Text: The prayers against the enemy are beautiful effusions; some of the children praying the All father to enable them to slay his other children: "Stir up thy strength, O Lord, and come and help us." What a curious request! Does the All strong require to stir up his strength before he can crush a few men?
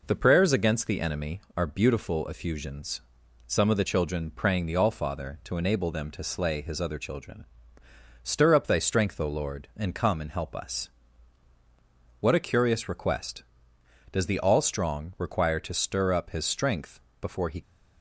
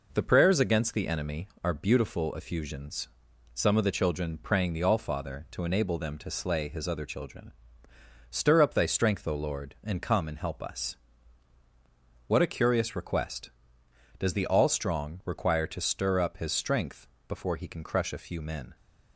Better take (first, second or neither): second